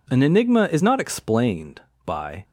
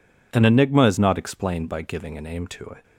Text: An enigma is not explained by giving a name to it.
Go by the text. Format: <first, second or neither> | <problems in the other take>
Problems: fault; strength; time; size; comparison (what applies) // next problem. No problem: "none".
second | stops before "giving a name to it"; at 2.4 s